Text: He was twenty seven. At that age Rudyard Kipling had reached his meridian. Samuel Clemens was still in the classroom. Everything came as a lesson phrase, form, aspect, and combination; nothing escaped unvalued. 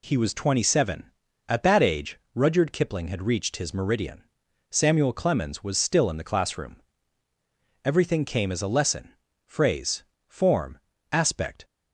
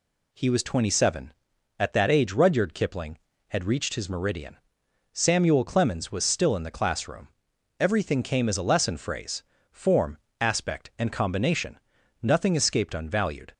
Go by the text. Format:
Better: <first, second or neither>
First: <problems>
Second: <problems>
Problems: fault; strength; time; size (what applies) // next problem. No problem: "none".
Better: second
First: pauses between "age" and "Rudyard"; slight; at 2.1 s; 0.16 s long // pauses between "lesson" and "phrase"; slight; at 9.1 s; 0.32 s long // stops before "and combination nothing escaped unvalued"; at 11.6 s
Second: none